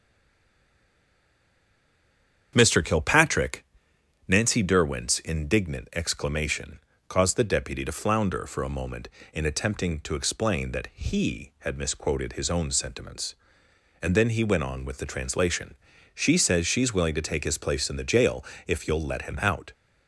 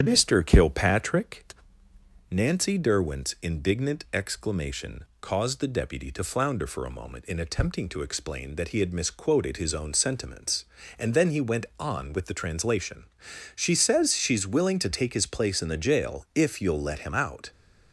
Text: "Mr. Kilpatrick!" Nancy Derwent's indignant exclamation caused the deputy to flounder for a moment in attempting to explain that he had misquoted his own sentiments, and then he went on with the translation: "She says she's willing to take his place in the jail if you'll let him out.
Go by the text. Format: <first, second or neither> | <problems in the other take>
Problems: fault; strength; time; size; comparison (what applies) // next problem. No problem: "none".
second | stays silent before the first word; until 2.5 s; 2.5 s long // starts louder than the rest; strong; until 3.5 s; 8.5 dB; strong in the second // pauses between "exclamation" and "caused"; slight; at 6.7 s; 0.30 s long; slight in the second // pauses between "jail" and "if"; slight; at 18.4 s; 0.24 s long